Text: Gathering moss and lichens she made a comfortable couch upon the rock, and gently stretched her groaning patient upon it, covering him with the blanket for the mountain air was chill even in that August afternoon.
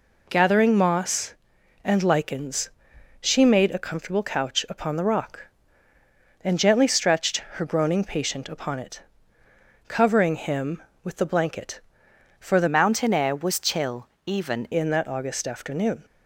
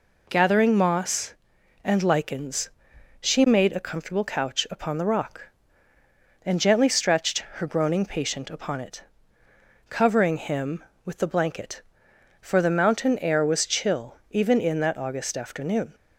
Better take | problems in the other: second | pauses between "lichens" and "she"; noticeable; at 2.6 s; 0.52 s long; noticeable in the second // pauses between "stretched" and "her"; slight; at 7.3 s; 0.16 s long; slight in the second // changes voice from "mountain" to "even"; from 12.6 to 14.6 s; 2.0 s long // pauses between "chill" and "even"; slight; at 14.0 s; 0.18 s long

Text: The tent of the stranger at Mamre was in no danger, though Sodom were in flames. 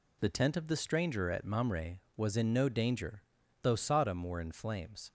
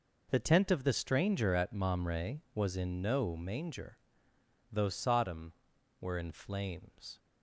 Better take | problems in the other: first | says "manger" for "danger"; at 3.3 s

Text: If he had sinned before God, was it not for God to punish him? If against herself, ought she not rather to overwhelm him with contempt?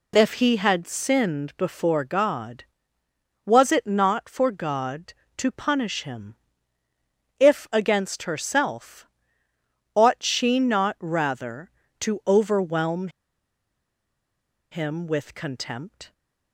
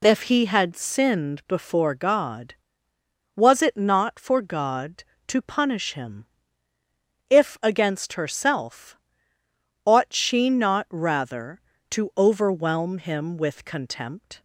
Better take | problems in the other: second | pauses between "overwhelm" and "him"; strong; at 13.0 s; 1.6 s long

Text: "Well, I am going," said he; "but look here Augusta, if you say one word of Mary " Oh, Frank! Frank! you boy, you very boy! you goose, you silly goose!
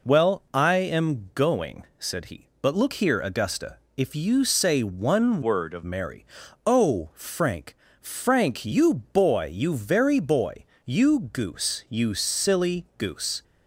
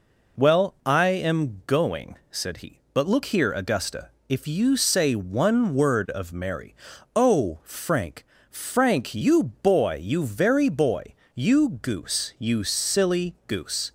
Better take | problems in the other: second | changes voice from "word" to "of"; from 5.4 to 5.8 s; 0.4 s long

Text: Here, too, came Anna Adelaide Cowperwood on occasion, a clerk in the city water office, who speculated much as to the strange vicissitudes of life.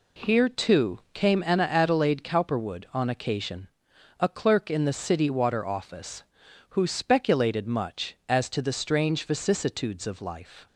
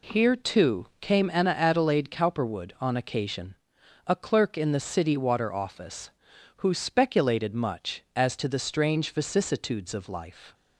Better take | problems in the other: neither | none

